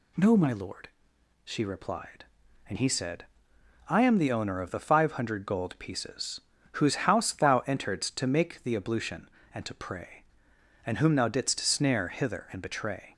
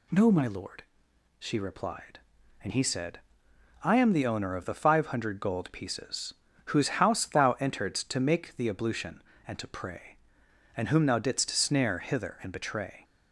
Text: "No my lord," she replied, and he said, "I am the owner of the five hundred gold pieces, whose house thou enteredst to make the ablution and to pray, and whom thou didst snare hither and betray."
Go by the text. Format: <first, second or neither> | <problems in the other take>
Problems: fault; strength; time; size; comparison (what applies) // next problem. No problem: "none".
neither | none